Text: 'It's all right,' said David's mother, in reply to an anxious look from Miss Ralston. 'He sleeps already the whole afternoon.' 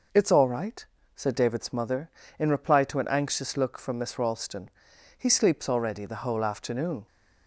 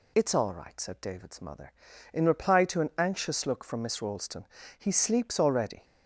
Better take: first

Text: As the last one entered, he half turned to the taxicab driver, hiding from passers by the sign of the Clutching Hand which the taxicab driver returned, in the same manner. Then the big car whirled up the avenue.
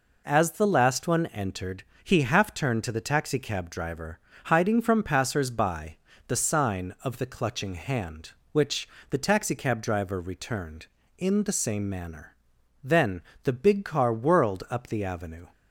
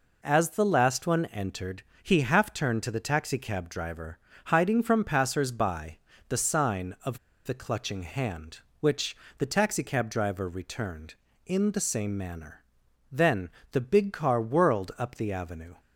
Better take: first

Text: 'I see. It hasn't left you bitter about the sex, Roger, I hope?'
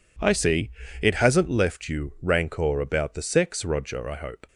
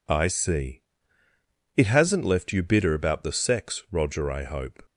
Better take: second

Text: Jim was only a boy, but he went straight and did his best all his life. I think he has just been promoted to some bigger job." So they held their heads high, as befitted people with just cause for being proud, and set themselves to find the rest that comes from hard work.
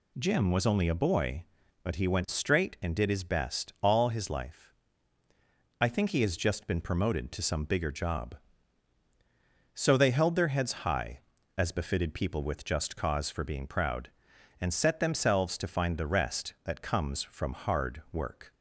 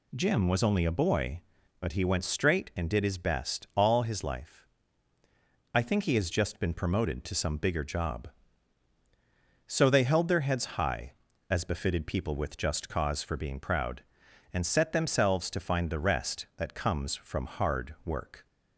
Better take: neither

